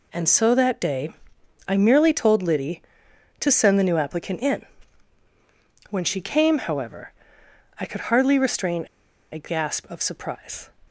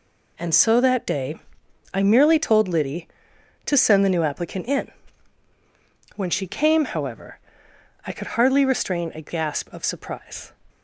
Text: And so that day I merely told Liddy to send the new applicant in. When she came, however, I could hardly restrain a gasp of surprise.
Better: second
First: pauses between "day" and "I"; noticeable; at 1.1 s; 0.56 s long // pauses between "restrain" and "a"; noticeable; at 8.8 s; 0.47 s long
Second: pauses between "day" and "I"; noticeable; at 1.3 s; 0.56 s long

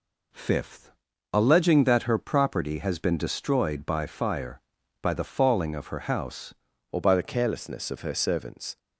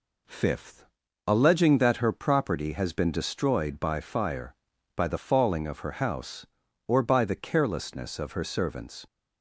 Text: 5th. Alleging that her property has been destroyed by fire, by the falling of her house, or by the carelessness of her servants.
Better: second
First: changes voice at "or"; from 6.9 s on; 1.8 s long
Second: none

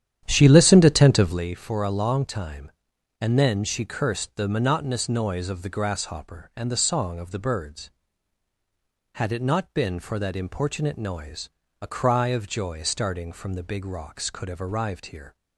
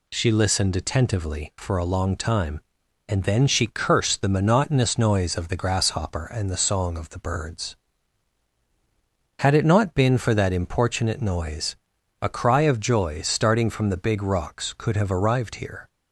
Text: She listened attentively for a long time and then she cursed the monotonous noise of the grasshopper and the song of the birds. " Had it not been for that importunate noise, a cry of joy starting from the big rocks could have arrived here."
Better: second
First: starts louder than the rest; strong; until 1.4 s; 11 dB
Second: none

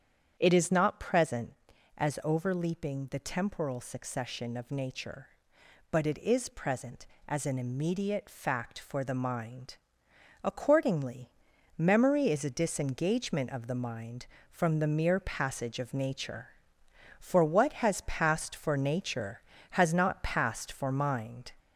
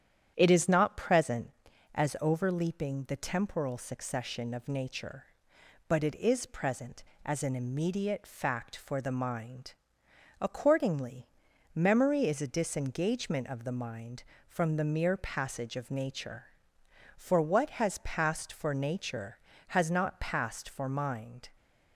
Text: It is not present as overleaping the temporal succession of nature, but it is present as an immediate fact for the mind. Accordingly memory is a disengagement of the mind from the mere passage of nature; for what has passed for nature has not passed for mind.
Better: second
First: gets louder; slight; throughout; 3 dB // starts louder than the rest; strong; until 1.4 s; 8.5 dB // pauses between "Accordingly" and "memory"; noticeable; at 11.3 s; 0.48 s long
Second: starts louder than the rest; strong; until 1.3 s; 9.5 dB // pauses between "Accordingly" and "memory"; noticeable; at 11.2 s; 0.48 s long

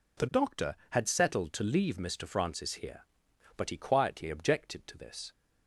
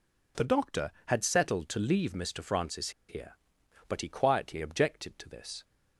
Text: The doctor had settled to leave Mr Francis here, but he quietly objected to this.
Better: first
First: none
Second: pauses between "Francis" and "here"; slight; at 2.8 s; 0.18 s long

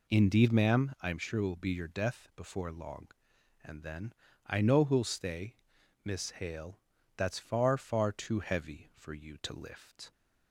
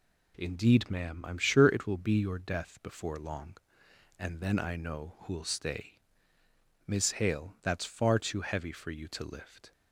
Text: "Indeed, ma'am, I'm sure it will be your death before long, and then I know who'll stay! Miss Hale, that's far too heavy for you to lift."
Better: second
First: pauses between "then" and "I"; slight; at 4.1 s; 0.32 s long // says "far" twice; at 7.7 s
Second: none

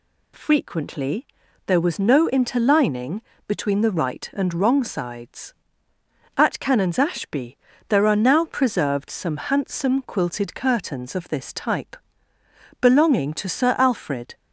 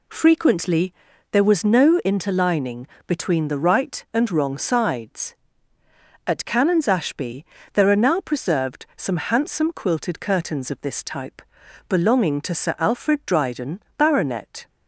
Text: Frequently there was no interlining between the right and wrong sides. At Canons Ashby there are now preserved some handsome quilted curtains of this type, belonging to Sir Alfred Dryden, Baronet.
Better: second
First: pauses between "Frequently" and "there"; at 1.2 s; 0.40 s long // pauses between "interlining" and "between"; slight; at 3.2 s; 0.26 s long // pauses between "Ashby" and "there"; slight; at 7.5 s; 0.30 s long // stops before "Dryden Baronet"; at 14.3 s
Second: pauses between "Frequently" and "there"; at 0.9 s; 0.38 s long // pauses between "interlining" and "between"; slight; at 2.8 s; 0.20 s long // pauses between "Ashby" and "there"; slight; at 7.4 s; 0.30 s long

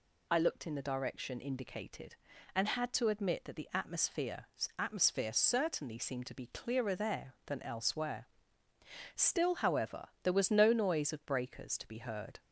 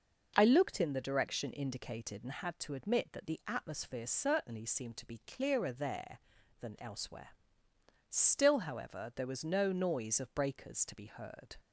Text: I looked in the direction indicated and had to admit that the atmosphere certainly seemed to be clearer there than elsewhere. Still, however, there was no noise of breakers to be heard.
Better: second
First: says "atmosphere" twice; at 4.7 s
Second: none

